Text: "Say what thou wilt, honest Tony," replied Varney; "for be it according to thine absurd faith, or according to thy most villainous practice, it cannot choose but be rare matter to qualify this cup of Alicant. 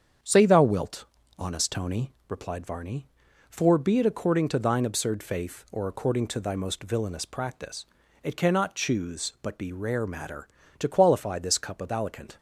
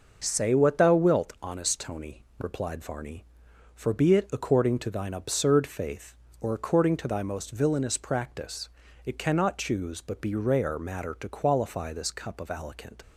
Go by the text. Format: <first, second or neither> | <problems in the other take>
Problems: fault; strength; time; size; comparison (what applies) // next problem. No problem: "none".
second | starts louder than the rest; strong; until 1.5 s; 7.5 dB // skips "what"; at 0.4 s